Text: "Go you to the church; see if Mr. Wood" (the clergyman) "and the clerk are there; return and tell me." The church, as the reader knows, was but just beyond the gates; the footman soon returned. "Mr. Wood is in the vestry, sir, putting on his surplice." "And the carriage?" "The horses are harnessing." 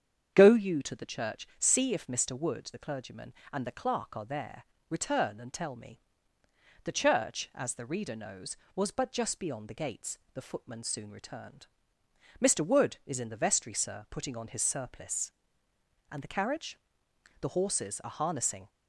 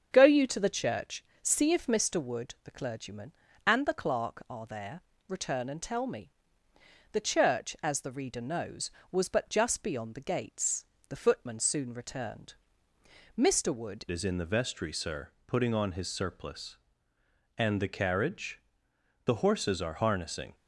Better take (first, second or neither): first